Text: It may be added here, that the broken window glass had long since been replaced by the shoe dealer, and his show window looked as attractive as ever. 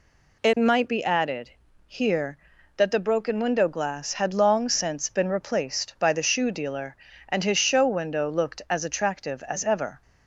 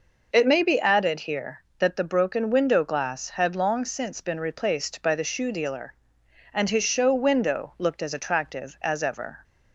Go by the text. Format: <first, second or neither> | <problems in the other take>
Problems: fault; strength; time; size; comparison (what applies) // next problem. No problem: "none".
second | says "might" for "may"; at 0.5 s // pauses between "added" and "here"; slight; at 1.5 s; 0.34 s long